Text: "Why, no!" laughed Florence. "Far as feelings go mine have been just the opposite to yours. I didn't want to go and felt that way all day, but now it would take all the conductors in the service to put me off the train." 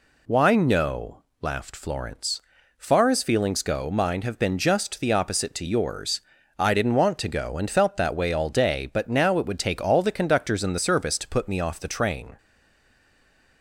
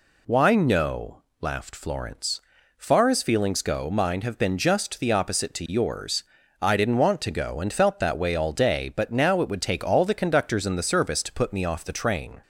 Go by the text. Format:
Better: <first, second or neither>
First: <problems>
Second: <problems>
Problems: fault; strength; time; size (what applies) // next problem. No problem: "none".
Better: second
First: stays silent after the last word; noticeable; from 12.3 s on; 1.3 s long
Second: none